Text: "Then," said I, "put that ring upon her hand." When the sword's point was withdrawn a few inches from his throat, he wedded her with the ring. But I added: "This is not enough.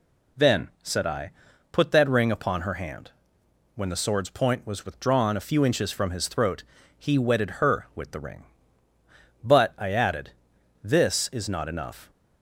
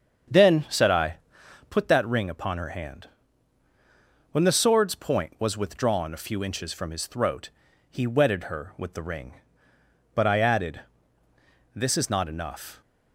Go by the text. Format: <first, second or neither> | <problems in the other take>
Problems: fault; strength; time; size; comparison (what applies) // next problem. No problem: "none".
first | starts louder than the rest; until 1.8 s; 7 dB